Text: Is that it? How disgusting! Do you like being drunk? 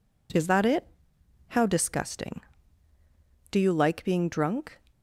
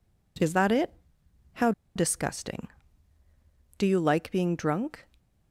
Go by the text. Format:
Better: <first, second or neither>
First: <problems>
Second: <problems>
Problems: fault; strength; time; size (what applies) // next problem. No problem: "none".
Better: first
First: none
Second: pauses between "How" and "disgusting"; slight; at 1.7 s; 0.24 s long